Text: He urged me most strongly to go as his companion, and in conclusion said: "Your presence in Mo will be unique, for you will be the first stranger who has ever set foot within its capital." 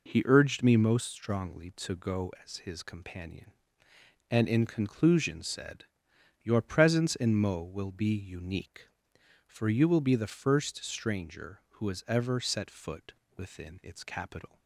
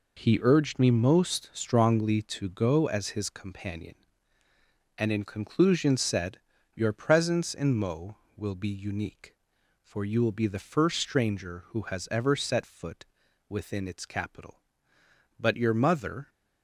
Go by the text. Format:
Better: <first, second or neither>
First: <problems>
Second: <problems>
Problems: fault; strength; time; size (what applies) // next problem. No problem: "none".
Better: first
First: pauses between "foot" and "within"; slight; at 13.1 s; 0.24 s long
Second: pauses between "foot" and "within"; at 13.0 s; 0.44 s long // goes on to say "But your mother"; noticeable; from 15.3 s on; 0.92 s long